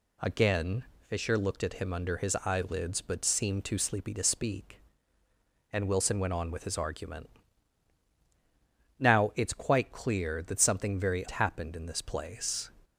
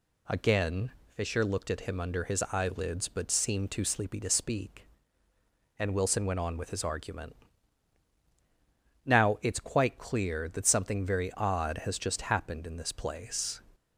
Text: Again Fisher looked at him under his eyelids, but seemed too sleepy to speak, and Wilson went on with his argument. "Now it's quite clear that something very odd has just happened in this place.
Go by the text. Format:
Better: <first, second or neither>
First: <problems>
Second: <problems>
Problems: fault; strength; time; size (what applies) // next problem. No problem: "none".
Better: second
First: pauses between "Again" and "Fisher"; slight; at 0.8 s; 0.24 s long // skips "odd has just"; at 11.2 s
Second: pauses between "Again" and "Fisher"; slight; at 0.9 s; 0.24 s long